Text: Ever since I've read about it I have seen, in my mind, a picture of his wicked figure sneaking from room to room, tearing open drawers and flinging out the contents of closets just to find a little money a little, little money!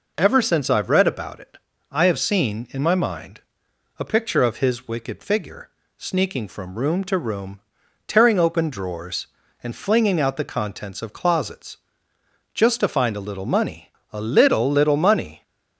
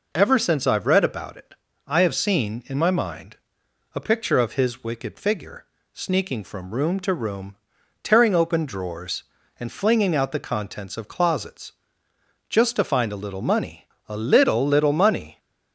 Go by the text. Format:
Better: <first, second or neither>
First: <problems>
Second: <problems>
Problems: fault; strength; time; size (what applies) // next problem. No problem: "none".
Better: neither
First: pauses between "it" and "I"; slight; at 1.5 s; 0.34 s long // pauses between "figure" and "sneaking"; slight; at 5.7 s; 0.26 s long // pauses between "closets" and "just"; noticeable; at 11.7 s; 0.76 s long // pauses between "money" and "a"; slight; at 13.8 s; 0.26 s long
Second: pauses between "it" and "I"; slight; at 1.5 s; 0.32 s long // pauses between "figure" and "sneaking"; slight; at 5.6 s; 0.26 s long // pauses between "closets" and "just"; noticeable; at 11.7 s; 0.76 s long // pauses between "money" and "a"; slight; at 13.8 s; 0.26 s long